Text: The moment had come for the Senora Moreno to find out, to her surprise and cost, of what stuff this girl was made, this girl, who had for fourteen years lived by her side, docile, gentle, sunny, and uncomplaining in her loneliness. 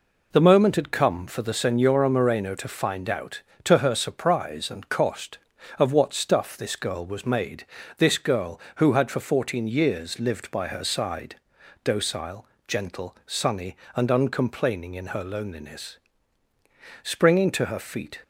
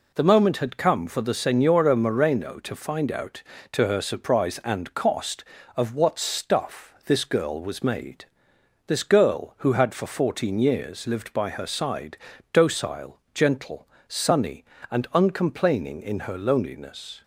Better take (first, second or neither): second